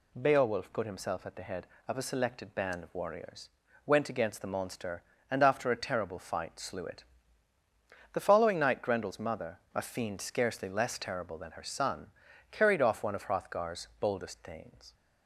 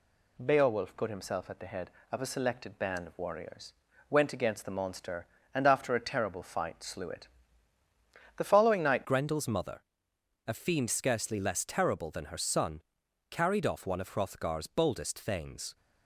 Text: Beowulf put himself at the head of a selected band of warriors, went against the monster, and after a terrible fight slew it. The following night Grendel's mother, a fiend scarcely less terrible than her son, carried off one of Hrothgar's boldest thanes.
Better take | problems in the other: first | changes voice at "Grendel's"; from 9.0 s on; 6.7 s long

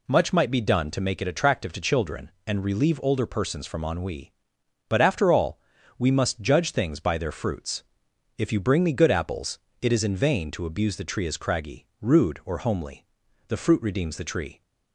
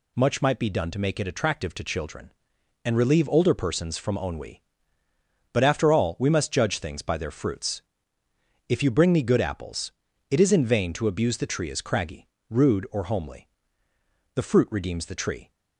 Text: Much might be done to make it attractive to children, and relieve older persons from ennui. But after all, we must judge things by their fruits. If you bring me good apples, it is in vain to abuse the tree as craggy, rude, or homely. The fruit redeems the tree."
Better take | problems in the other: neither | none

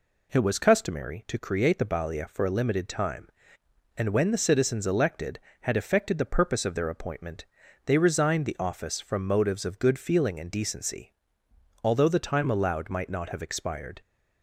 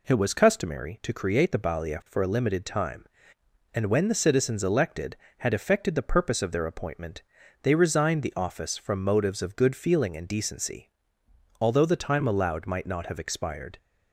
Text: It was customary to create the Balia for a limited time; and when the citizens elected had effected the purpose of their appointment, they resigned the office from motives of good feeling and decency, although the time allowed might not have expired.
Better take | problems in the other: neither | none

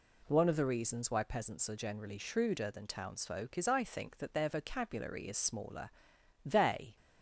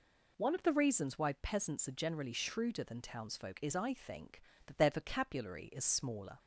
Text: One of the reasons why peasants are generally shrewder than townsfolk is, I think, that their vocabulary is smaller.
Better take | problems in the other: second | goes on to say "They"; from 6.4 s on; 0.50 s long

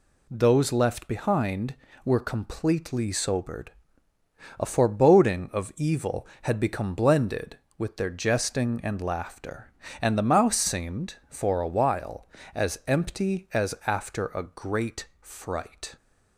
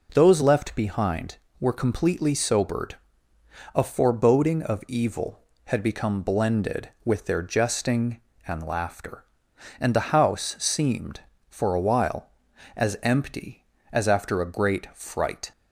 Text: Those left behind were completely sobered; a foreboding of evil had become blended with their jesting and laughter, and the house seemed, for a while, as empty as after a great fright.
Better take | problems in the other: second | says "mouse" for "house"; at 10.3 s

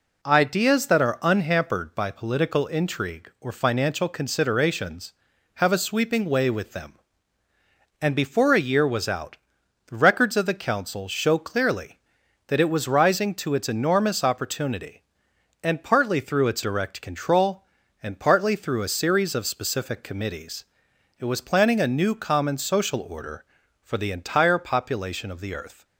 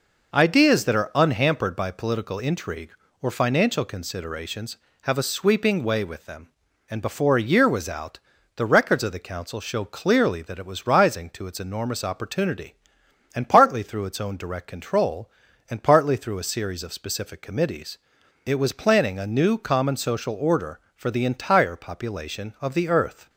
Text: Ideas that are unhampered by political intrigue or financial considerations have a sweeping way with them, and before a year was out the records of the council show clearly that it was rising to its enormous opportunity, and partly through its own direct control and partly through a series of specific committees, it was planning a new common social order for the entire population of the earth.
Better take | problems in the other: second | pauses between "out" and "the"; noticeable; at 9.3 s; 0.50 s long; also in the second // skips "own"; at 16.6 s

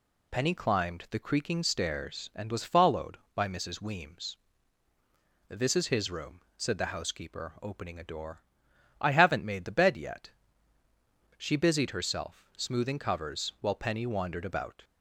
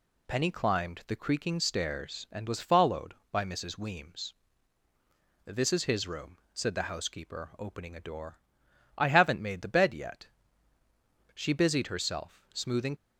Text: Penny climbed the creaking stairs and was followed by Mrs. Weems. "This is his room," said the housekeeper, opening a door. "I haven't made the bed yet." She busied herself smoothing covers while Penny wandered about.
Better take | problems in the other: first | stops before "covers while Penny wandered about"; at 12.9 s

